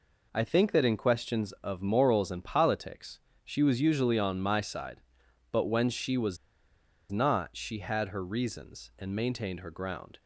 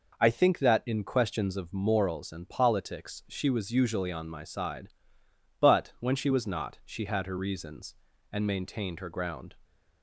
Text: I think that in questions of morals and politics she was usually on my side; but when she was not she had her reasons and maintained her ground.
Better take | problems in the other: second | pauses between "politics" and "she"; slight; at 3.1 s; 0.24 s long // pauses between "was" and "not"; noticeable; at 6.3 s; 0.73 s long

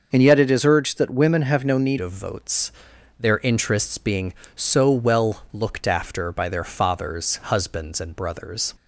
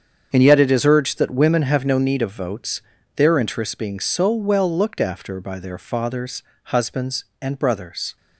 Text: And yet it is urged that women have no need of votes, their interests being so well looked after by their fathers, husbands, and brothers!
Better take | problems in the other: second | starts louder than the rest; noticeable; until 1.1 s; 6 dB; strong in the second // changes voice at "of"; from 1.9 s on; 6.8 s long

